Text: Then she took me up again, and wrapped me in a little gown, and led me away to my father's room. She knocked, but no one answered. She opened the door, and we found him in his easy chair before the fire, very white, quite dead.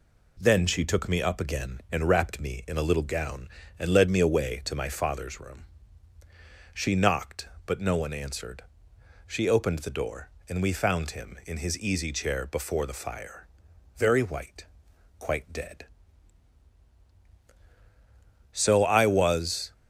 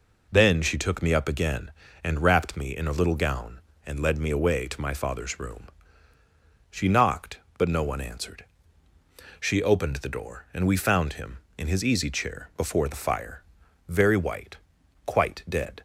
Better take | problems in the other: second | goes on to say "So I was"; noticeable; from 18.5 s on; 1.2 s long

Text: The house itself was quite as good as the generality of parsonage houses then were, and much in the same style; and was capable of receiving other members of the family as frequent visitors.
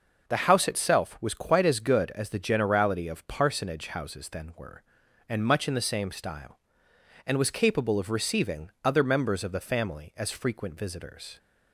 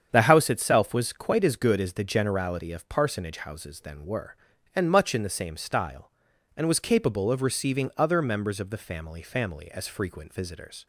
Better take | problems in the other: first | starts louder than the rest; strong; until 1.1 s; 8 dB // says "family" twice; at 9.2 s

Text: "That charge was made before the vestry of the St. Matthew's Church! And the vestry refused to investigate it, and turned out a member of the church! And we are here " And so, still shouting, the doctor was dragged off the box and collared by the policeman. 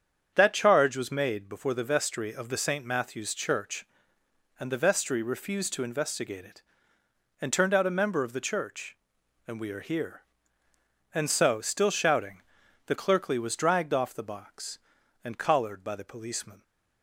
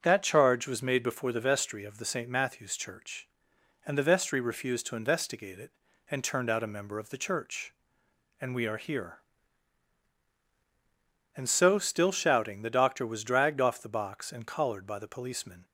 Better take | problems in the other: second | starts louder than the rest; strong; until 1.3 s; 8 dB; strong in the second // says "clerkly" for "doctor"; at 12.9 s

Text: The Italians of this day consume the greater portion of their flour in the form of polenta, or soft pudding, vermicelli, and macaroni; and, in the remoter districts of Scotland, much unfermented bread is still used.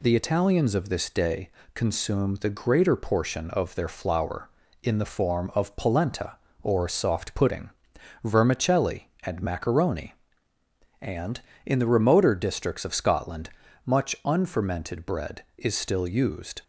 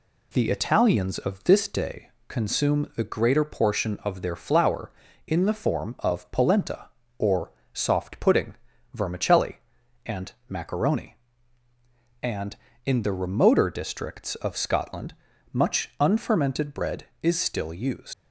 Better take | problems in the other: first | pauses between "day" and "consume"; slight; at 2.0 s; 0.20 s long; slight in the first // pauses between "or" and "soft"; slight; at 7.5 s; 0.22 s long // pauses between "and" and "macaroni"; slight; at 10.3 s; 0.16 s long // leaves "used" unfinished; at 18.1 s; 90 ms

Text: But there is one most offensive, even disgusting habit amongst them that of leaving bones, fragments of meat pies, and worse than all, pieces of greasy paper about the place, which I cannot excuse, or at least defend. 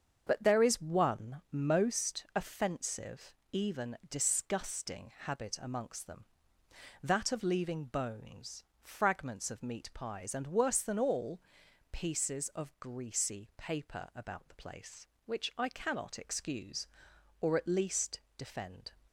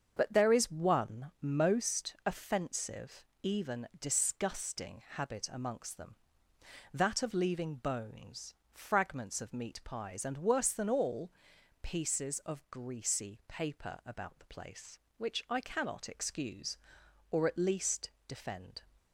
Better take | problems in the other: neither | starts louder than the rest; the same in both // pauses between "least" and "defend"; slight; the same in both

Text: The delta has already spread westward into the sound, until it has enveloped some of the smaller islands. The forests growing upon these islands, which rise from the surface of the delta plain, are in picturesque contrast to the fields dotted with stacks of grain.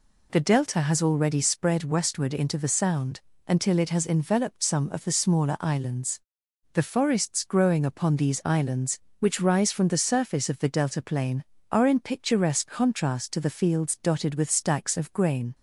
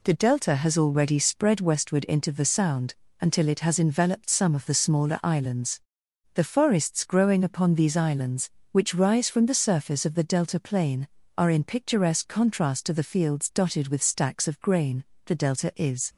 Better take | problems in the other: first | goes on to say "The delta is"; noticeable; from 15.2 s on; 0.84 s long

